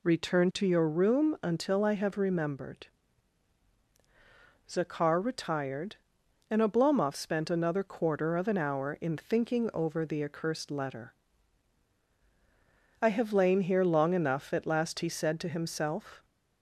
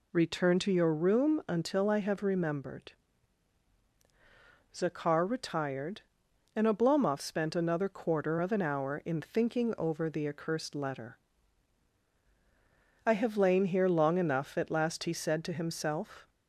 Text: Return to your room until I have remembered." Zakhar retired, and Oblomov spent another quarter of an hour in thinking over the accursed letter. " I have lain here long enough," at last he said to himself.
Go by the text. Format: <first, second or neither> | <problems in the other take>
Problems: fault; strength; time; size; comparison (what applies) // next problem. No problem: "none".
neither | none